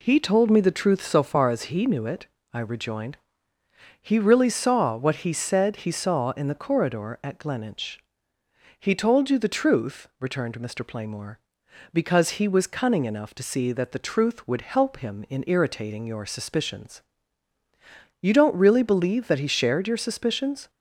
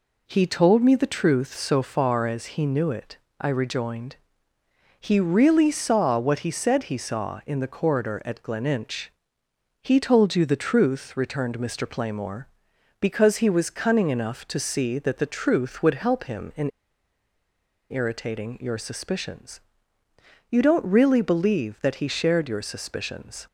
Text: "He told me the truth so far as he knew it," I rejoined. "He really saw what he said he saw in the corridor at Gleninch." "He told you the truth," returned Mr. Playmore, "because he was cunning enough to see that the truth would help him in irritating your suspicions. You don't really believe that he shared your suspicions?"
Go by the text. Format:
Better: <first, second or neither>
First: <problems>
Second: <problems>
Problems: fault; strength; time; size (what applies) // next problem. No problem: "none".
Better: first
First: none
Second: pauses between "in" and "irritating"; at 16.7 s; 1.2 s long